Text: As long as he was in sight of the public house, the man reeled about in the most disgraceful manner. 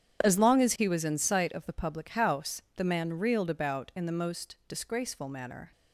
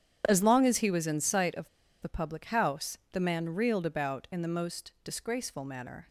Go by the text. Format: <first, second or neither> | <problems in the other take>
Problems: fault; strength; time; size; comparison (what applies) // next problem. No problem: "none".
first | starts louder than the rest; strong; until 1.2 s; 9.5 dB; strong in the first // pauses between "of" and "the"; slight; at 1.6 s; 0.34 s long